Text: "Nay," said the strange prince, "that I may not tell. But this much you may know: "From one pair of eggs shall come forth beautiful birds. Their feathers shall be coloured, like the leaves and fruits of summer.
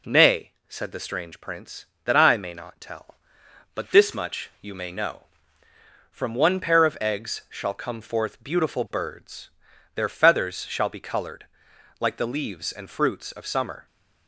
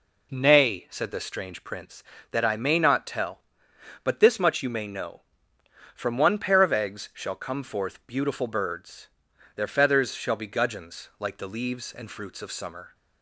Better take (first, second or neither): first